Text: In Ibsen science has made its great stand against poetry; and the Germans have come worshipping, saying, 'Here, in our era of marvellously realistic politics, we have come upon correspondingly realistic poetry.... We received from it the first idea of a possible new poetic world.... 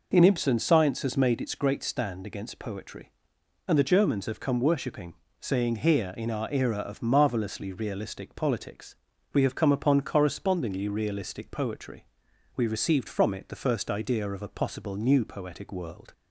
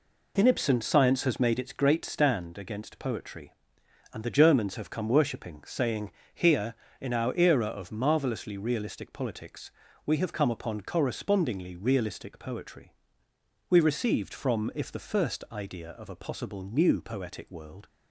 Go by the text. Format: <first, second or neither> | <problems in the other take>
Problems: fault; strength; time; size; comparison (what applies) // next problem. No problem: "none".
first | says "if" for "it"; at 14.7 s